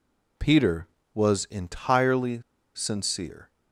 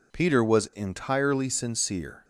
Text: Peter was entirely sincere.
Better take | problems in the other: second | pauses between "entirely" and "sincere"; slight; at 2.4 s; 0.34 s long

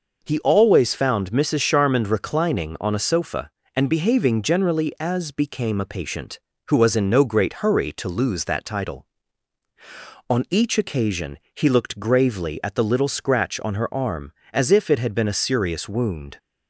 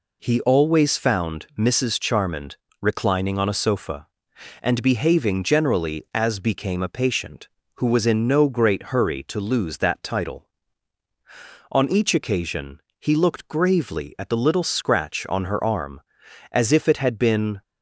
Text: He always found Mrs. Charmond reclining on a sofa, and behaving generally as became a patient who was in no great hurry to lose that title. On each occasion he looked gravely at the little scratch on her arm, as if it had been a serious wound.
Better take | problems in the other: first | pauses between "Charmond" and "reclining"; slight; at 2.5 s; 0.26 s long // pauses between "occasion" and "he"; slight; at 12.8 s; 0.18 s long; slight in the first // stops before "a serious wound"; at 17.6 s

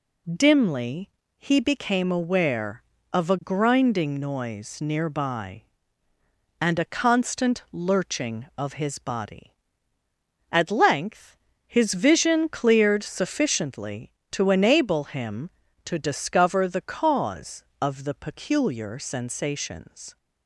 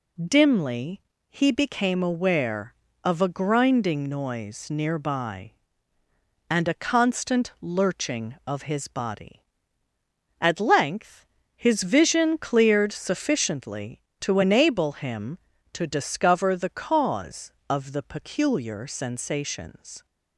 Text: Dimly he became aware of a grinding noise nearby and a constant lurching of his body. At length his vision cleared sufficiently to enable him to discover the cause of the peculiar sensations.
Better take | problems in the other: neither | pauses between "Dimly" and "he"; slight; the same in both // pauses between "length" and "his"; slight; the same in both

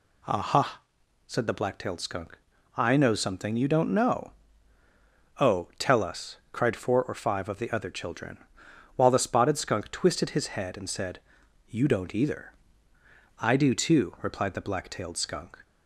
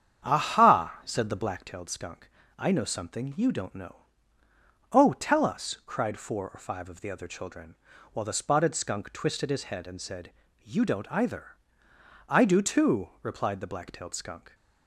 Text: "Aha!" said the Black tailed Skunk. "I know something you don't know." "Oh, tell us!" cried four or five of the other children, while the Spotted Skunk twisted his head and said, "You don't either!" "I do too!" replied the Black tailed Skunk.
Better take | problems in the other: first | starts louder than the rest; strong; until 1.7 s; 8.5 dB

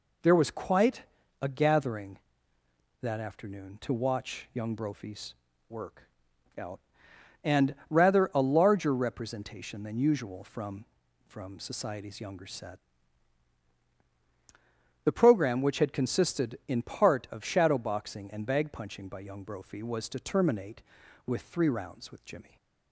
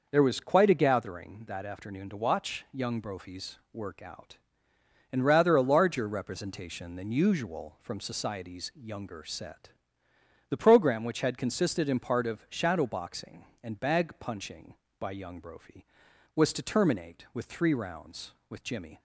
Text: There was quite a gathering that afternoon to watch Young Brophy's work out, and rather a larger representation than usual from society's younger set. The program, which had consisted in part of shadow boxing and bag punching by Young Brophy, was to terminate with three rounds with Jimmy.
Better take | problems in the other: second | pauses between "quite" and "a"; at 1.0 s; 0.38 s long // pauses between "Brophy's" and "work"; slight; at 5.3 s; 0.34 s long; slight in the second // pauses between "work" and "out"; noticeable; at 6.0 s; 0.56 s long // pauses between "and" and "rather"; slight; at 7.7 s; 0.16 s long // says "from" twice; at 11.2 s // stays silent after the last word; slight; from 22.4 s on; 0.5 s long

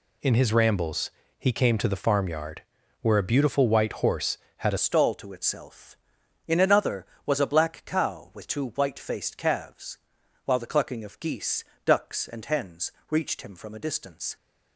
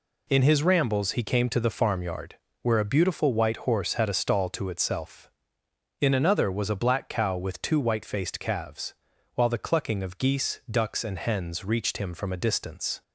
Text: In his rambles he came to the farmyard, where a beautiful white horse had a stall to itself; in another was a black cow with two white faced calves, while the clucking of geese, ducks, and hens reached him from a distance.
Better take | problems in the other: second | pauses between "rambles" and "he"; slight; at 1.1 s; 0.28 s long // changes voice at "stall"; from 4.7 s on; 9.6 s long // pauses between "hens" and "reached"; slight; at 12.9 s; 0.18 s long

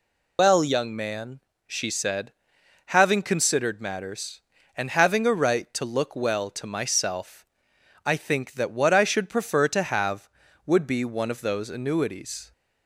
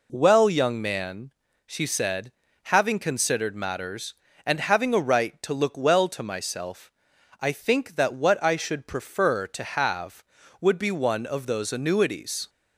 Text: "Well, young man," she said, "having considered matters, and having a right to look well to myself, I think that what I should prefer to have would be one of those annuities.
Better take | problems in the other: second | loses the start of "Well"; at 0.3 s; 115 ms

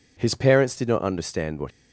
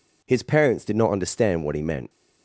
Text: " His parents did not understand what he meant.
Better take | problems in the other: second | stops before "he meant"; at 1.6 s

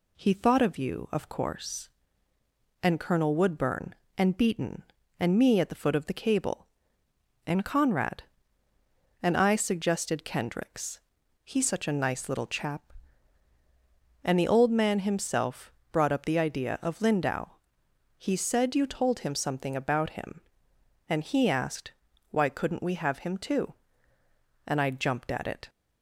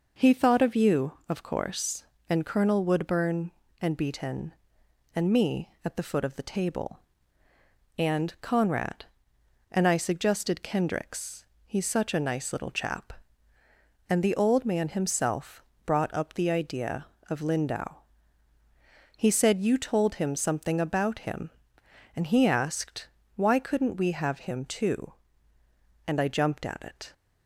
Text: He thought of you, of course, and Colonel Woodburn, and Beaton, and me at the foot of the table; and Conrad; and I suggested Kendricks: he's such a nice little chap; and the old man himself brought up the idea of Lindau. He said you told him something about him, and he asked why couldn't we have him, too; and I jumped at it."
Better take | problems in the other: second | says "cable" for "table"; at 6.1 s // pauses between "himself" and "brought"; slight; at 15.7 s; 0.22 s long; slight in the second // pauses between "asked" and "why"; at 21.9 s; 0.38 s long; slight in the second

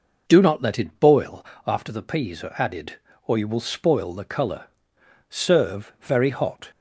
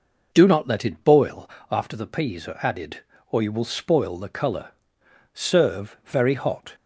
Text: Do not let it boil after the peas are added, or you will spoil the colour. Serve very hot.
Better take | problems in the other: neither | pauses between "boil" and "after"; slight; the same in both

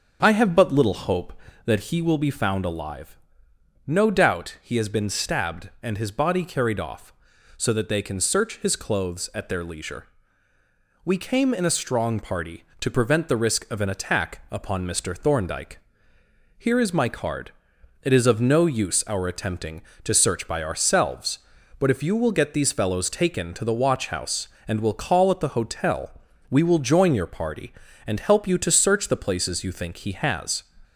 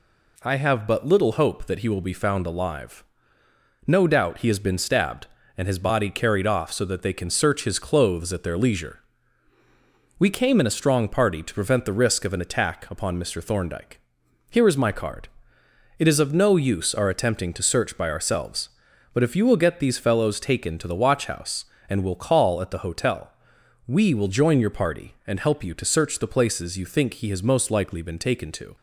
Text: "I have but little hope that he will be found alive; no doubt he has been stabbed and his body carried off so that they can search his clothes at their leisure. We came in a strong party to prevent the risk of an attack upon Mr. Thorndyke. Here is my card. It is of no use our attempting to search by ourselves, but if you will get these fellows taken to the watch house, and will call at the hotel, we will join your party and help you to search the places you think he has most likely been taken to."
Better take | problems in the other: second | starts louder than the rest; until 1.2 s; 6.5 dB // stops before "most likely been taken to"; at 30.8 s

